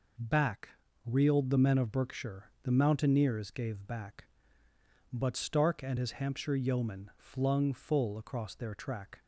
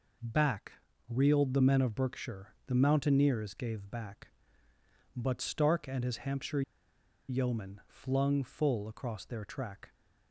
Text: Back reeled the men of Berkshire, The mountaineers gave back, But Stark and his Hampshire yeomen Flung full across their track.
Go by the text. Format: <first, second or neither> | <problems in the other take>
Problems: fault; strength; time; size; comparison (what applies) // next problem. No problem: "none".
first | pauses between "Back" and "reeled"; slight; at 0.7 s; 0.36 s long; slight in the first // pauses between "Hampshire" and "yeomen"; noticeable; at 6.6 s; 0.67 s long